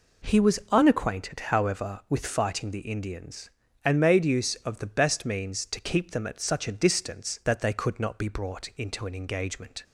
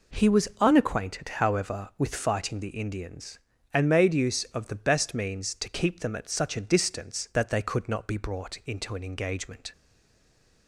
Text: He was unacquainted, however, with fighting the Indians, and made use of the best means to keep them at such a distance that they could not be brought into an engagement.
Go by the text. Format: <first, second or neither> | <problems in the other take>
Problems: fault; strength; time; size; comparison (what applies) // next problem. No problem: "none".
first | stays silent after the last word; slight; from 9.7 s on; 0.9 s long